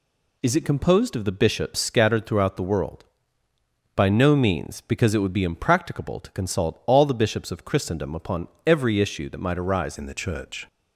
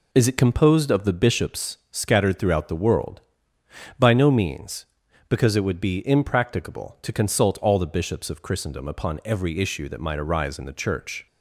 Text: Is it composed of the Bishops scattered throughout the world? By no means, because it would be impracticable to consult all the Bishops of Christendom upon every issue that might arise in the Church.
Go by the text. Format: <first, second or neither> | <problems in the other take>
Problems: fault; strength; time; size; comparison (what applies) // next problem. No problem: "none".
second | pauses between "upon" and "every"; slight; at 8.4 s; 0.18 s long // changes voice at "in"; from 9.9 s on; 0.7 s long